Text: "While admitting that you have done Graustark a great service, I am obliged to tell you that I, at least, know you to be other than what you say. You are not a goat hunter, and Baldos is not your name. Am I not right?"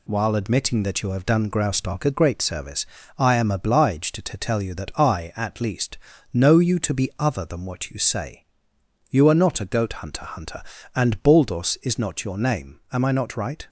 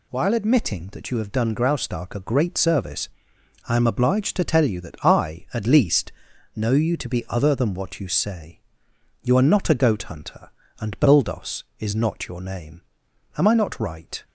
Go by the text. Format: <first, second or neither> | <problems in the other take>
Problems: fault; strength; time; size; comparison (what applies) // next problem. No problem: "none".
second | says "hunter" twice; at 10.2 s